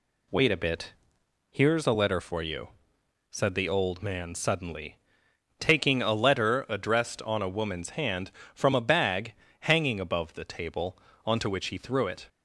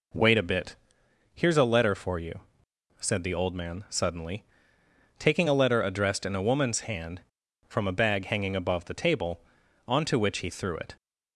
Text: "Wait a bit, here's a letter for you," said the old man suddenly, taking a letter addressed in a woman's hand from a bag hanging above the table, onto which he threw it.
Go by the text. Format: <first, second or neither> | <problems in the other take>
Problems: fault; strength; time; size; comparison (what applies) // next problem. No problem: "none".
second | says "on" for "in"; at 7.2 s // pauses between "bag" and "hanging"; slight; at 9.3 s; 0.26 s long